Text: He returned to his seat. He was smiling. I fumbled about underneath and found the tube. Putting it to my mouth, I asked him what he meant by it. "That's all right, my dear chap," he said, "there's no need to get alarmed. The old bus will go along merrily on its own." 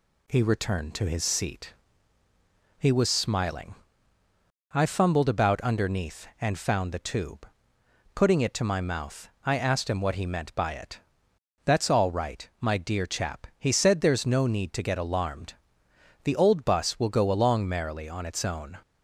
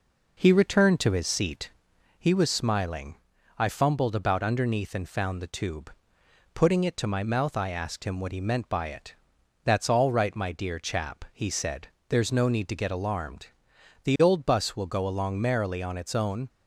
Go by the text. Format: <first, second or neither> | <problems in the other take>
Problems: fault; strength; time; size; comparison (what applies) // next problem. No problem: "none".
first | starts louder than the rest; noticeable; until 1.9 s; 4.5 dB